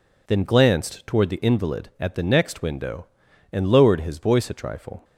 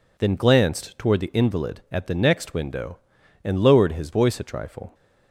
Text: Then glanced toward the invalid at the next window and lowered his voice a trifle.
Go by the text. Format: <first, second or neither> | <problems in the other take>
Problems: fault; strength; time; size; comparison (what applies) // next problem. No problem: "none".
neither | none